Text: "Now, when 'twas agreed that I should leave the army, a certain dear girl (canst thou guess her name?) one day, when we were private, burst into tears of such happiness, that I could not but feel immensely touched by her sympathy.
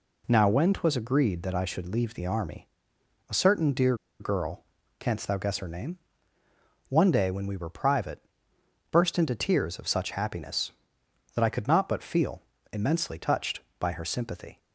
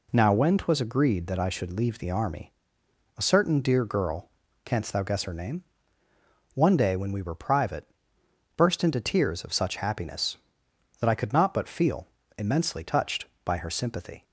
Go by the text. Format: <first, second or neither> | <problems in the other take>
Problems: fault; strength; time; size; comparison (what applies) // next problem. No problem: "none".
second | pauses between "dear" and "girl"; slight; at 3.9 s; 0.24 s long // pauses between "feel" and "immensely"; slight; at 12.3 s; 0.32 s long; slight in the second